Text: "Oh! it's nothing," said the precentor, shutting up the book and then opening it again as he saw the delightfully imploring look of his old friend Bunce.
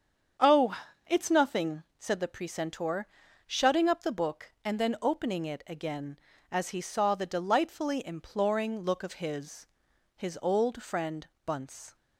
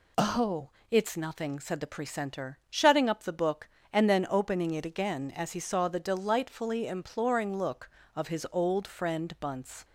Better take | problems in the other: second | starts louder than the rest; strong; until 1.7 s; 7.5 dB // says "his" twice; at 10.1 s // pauses between "friend" and "Bunce"; slight; at 11.2 s; 0.20 s long

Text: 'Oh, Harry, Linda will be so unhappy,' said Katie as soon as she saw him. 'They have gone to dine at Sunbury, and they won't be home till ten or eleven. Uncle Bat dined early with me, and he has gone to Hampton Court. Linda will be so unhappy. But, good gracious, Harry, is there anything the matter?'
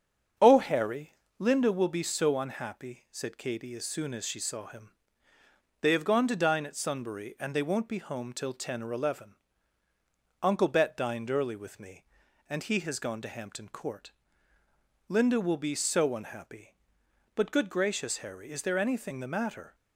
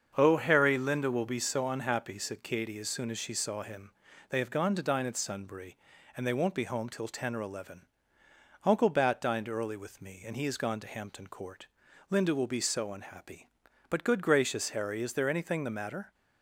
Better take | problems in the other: second | starts louder than the rest; strong; until 1.6 s; 7.5 dB; also in the second // says "Bet" for "Bat"; at 10.6 s

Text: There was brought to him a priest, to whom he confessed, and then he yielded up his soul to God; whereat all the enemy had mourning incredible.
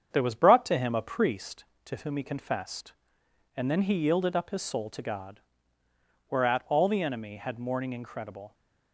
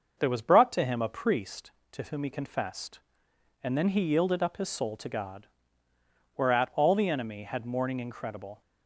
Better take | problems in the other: second | gets quieter; slight; throughout; 2 dB // starts louder than the rest; strong; until 1.1 s; 7.5 dB; noticeable in the second

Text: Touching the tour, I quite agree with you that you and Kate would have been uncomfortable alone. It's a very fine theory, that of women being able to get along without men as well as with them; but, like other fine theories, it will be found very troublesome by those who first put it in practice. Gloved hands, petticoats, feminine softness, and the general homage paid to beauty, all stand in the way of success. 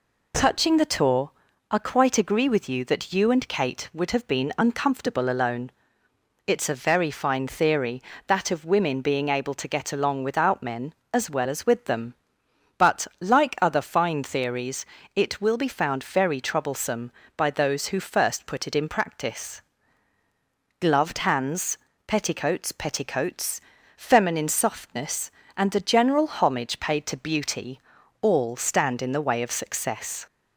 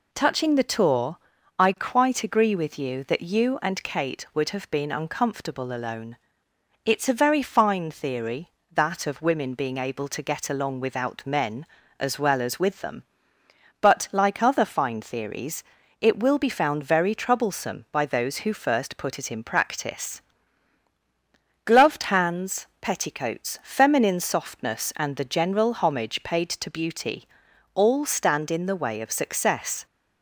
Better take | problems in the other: second | says "petticoats" twice; at 22.7 s

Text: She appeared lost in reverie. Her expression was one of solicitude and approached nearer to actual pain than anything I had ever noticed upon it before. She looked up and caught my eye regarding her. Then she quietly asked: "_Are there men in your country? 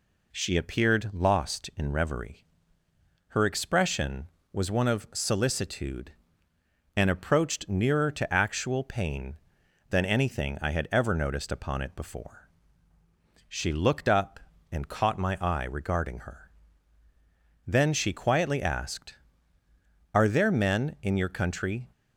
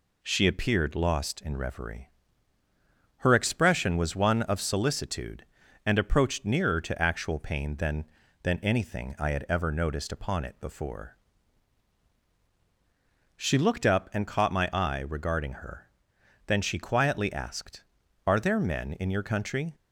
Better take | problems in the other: first | says "than" twice; at 8.4 s

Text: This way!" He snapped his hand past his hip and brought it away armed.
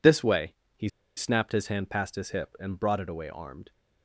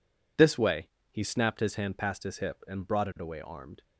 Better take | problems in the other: second | pauses between "He" and "snapped"; slight; at 0.8 s; 0.27 s long

